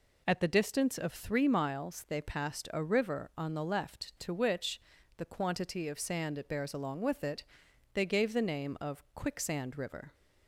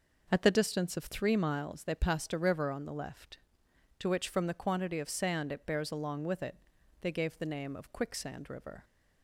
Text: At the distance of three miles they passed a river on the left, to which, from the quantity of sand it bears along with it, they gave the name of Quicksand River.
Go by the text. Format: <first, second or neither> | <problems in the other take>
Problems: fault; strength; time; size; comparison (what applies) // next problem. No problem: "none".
second | skips "from"; at 4.9 s